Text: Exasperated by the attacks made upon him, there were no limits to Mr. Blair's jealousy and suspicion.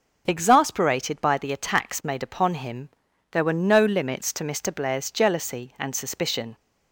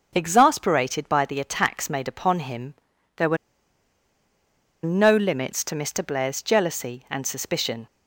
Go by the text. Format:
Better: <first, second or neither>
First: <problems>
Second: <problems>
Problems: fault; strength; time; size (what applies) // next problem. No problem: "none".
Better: first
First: none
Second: pauses between "were" and "no"; strong; at 3.3 s; 1.4 s long